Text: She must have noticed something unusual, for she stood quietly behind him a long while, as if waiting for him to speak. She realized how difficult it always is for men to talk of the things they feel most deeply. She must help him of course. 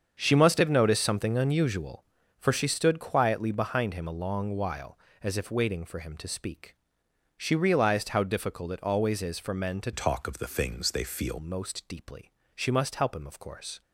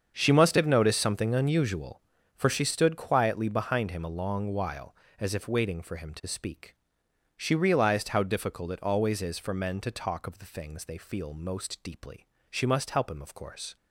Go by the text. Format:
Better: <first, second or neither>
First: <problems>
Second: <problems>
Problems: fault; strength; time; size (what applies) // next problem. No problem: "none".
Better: second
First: starts louder than the rest; strong; until 1.2 s; 7 dB // changes voice from "talk" to "feel"; from 9.9 to 11.3 s; 1.4 s long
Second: starts louder than the rest; strong; until 1.1 s; 7 dB